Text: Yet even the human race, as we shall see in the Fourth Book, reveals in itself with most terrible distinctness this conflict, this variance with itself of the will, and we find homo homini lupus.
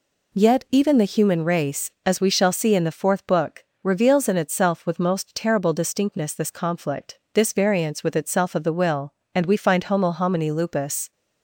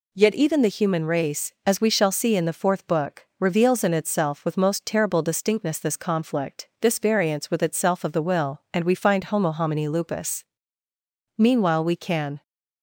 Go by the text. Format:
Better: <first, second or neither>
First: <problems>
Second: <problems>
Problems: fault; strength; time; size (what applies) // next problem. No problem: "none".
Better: first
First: none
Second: goes on to say "Meanwhile we can"; noticeable; from 11.3 s on; 1.0 s long